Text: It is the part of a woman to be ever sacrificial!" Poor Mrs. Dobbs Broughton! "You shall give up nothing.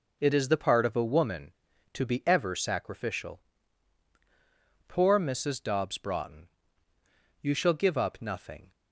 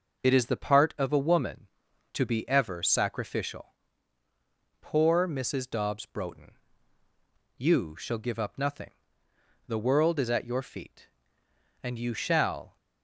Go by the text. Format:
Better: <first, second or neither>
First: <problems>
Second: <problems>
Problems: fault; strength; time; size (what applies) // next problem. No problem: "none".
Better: first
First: none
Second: goes on to say "The world is at your feet and you shall"; strong; from 9.6 s on; 3.0 s long